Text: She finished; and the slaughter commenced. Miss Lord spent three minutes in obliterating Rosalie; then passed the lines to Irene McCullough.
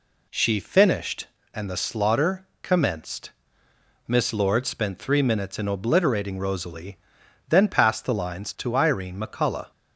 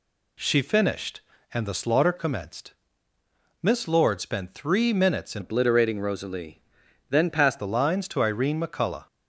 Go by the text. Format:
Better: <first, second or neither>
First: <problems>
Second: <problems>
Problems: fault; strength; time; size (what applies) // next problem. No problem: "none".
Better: first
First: none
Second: changes voice from "obliterating" to "passed"; from 5.4 to 7.5 s; 2.1 s long